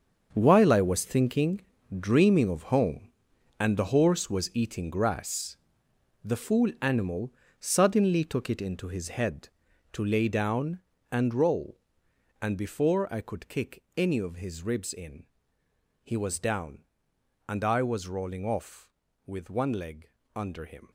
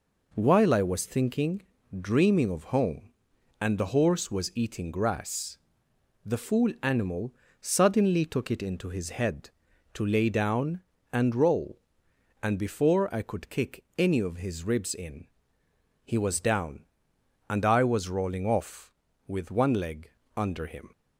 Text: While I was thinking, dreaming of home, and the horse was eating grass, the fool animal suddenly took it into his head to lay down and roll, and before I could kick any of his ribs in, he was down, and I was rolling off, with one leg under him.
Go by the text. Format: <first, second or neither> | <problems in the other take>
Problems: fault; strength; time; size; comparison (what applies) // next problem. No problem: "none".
second | gets quieter; strong; throughout; 12.5 dB // pauses between "animal" and "suddenly"; slight; at 7.3 s; 0.26 s long; slight in the second // pauses between "leg" and "under"; slight; at 20.1 s; 0.26 s long; slight in the second